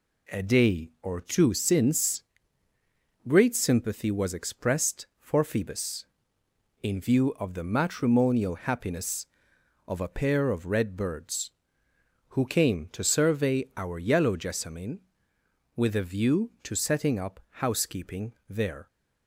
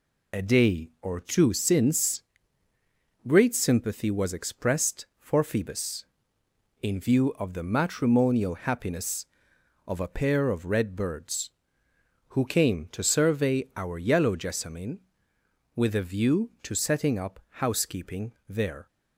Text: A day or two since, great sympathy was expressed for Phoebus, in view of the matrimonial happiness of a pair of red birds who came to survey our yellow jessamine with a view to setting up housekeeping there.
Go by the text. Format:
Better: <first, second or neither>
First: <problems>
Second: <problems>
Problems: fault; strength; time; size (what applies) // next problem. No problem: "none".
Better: first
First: pauses between "housekeeping" and "there"; slight; at 18.3 s; 0.18 s long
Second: loses the start of "A"; at 0.3 s; 55 ms // pauses between "housekeeping" and "there"; slight; at 18.3 s; 0.18 s long